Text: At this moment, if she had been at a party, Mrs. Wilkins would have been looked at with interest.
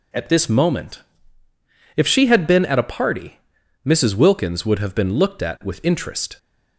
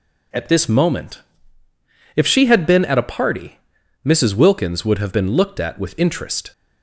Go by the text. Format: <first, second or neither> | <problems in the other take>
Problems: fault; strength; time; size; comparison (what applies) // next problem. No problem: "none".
neither | none